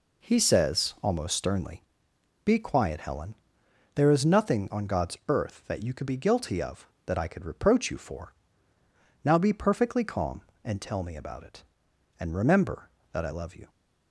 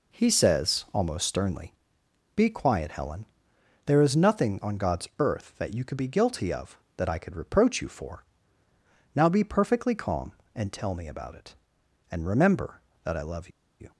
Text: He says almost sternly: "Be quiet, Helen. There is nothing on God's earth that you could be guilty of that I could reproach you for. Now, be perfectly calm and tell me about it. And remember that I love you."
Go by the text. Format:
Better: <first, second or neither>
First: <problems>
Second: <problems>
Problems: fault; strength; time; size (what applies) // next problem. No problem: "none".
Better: first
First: none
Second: pauses between "love" and "you"; slight; at 13.4 s; 0.31 s long